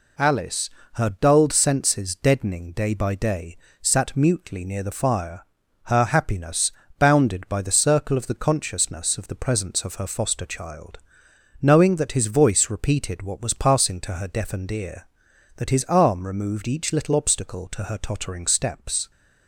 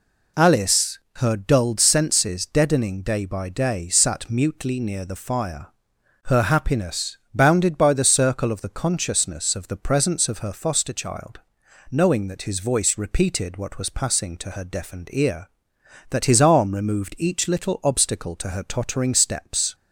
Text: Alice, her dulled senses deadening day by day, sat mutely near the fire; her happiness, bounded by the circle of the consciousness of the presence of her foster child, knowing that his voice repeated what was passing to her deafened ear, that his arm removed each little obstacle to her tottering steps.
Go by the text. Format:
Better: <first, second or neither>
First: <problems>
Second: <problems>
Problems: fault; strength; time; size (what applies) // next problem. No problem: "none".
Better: neither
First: none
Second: none